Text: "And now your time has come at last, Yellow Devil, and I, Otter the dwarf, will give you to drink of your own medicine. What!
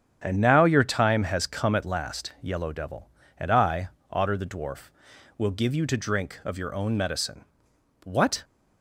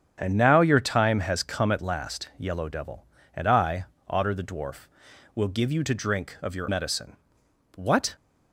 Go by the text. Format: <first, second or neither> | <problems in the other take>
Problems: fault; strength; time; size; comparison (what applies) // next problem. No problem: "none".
first | starts louder than the rest; strong; until 1.1 s; 7.5 dB; strong in the first // skips "own"; at 6.6 s